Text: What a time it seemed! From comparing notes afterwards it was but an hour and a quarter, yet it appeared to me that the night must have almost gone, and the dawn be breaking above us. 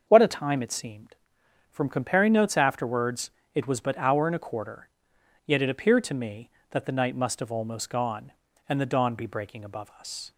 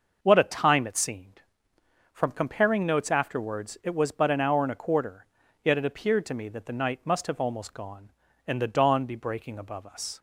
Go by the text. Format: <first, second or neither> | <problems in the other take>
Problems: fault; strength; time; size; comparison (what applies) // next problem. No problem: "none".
second | starts louder than the rest; until 1.0 s; 6.5 dB; noticeable in the second // pauses between "afterwards" and "it"; slight; at 3.2 s; 0.24 s long // skips "an"; at 3.9 s